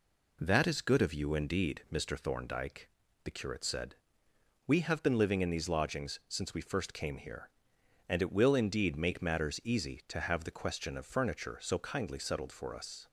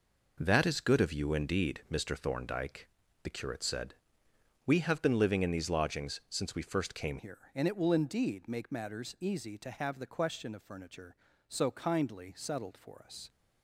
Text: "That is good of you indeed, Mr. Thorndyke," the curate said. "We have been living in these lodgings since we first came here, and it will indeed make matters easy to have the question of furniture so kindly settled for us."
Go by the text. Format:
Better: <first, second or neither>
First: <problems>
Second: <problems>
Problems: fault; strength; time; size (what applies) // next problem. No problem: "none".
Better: first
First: none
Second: changes voice at "here"; from 7.1 s on; 6.1 s long